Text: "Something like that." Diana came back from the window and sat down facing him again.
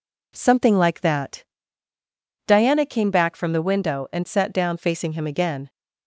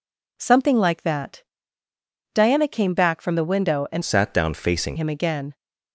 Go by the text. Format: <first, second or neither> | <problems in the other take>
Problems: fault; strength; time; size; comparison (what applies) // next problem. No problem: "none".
first | changes voice from "sat" to "facing"; from 4.0 to 4.9 s; 0.9 s long